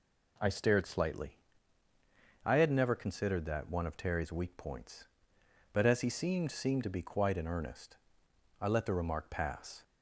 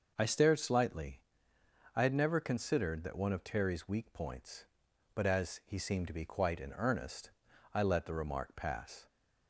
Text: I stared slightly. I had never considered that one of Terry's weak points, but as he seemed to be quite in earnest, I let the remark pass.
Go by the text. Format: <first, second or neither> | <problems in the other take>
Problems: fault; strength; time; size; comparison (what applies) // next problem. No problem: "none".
second | says "seemed" twice; at 6.5 s